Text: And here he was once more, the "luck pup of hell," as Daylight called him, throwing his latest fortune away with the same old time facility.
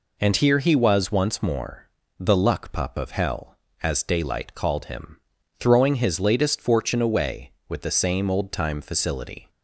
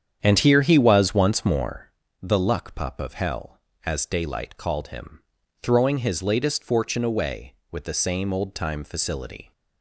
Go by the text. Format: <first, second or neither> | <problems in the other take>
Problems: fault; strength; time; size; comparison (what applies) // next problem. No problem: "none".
first | starts louder than the rest; strong; until 1.9 s; 8.5 dB